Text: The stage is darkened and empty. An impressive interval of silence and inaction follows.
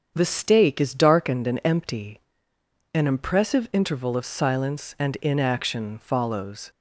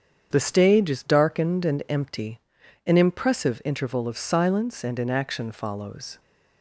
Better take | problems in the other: second | starts louder than the rest; strong; until 1.1 s; 7.5 dB; strong in the second // says "stake" for "stage"; at 0.2 s

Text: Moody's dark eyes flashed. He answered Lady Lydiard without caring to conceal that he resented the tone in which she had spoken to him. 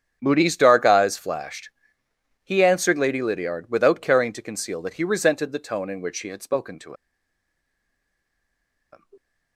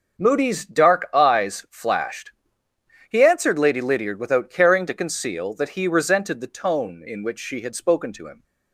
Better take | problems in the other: second | starts louder than the rest; strong; until 1.2 s; 8.5 dB; also in the second // pauses between "to" and "him"; strong; at 6.9 s; 1.9 s long

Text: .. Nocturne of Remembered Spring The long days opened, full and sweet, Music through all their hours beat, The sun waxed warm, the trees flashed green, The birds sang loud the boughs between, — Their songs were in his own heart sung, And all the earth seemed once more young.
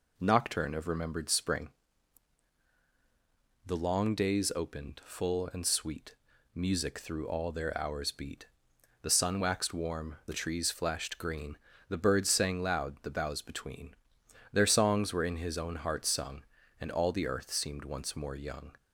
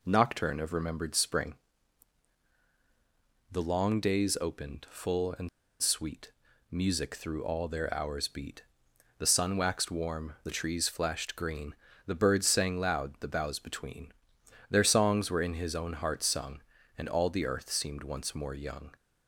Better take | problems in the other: first | pauses between "Spring" and "The"; strong; at 1.5 s; 1.9 s long; strong in the first // pauses between "and" and "sweet"; slight; at 5.4 s; 0.33 s long

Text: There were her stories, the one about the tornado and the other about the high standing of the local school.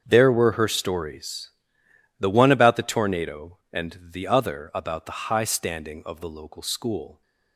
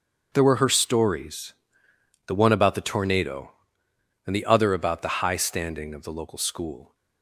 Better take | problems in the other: neither | starts louder than the rest; the same in both

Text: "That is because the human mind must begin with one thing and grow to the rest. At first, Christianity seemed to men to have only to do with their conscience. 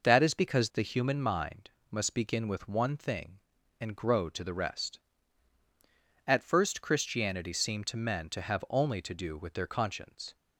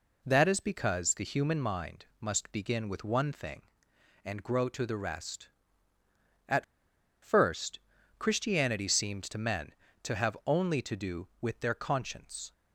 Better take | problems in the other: first | pauses between "mind" and "must"; slight; at 2.0 s; 0.16 s long; slight in the first // pauses between "At" and "first"; noticeable; at 6.6 s; 0.57 s long

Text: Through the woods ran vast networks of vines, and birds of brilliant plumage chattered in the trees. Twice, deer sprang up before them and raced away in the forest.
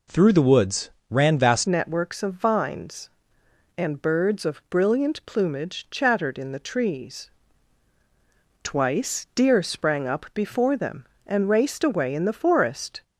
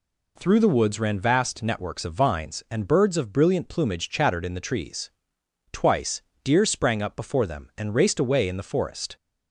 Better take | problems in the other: second | pauses between "woods" and "ran"; slight; at 0.8 s; 0.20 s long // changes voice at "networks"; from 1.6 s on; 11.4 s long

